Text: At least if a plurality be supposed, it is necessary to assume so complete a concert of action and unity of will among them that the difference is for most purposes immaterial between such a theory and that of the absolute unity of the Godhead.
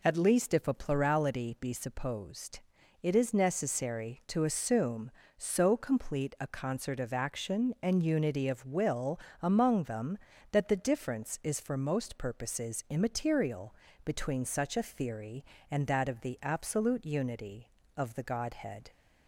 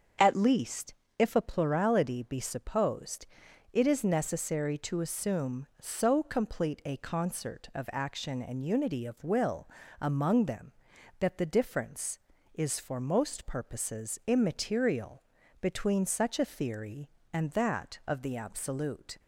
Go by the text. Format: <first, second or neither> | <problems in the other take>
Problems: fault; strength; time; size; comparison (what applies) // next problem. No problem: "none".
first | starts louder than the rest; until 1.4 s; 7 dB // pauses between "least" and "if"; slight; at 0.9 s; 0.24 s long // pauses between "will" and "among"; slight; at 9.6 s; 0.32 s long; slight in the first // pauses between "immaterial" and "between"; at 15.2 s; 0.38 s long; slight in the first // stops before "unity of the Godhead"; at 19.1 s